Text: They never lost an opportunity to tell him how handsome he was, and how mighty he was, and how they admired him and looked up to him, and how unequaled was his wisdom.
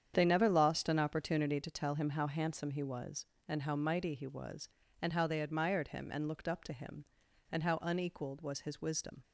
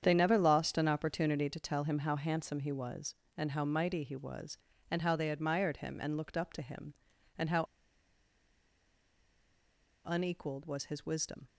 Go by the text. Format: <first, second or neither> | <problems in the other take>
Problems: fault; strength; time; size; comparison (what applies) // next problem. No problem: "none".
first | starts louder than the rest; strong; until 1.0 s; 8.5 dB; strong in the first // pauses between "how" and "unequaled"; strong; at 7.6 s; 2.4 s long